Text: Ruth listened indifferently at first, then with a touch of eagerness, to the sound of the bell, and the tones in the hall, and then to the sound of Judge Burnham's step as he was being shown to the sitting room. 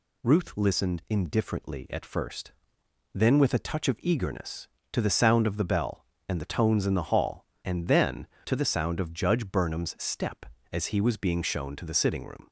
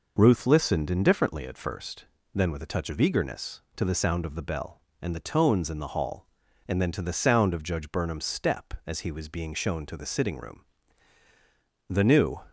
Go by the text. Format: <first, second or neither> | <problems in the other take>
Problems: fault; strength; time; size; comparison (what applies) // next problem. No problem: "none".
first | goes on to say "The new"; from 11.8 s on; 0.54 s long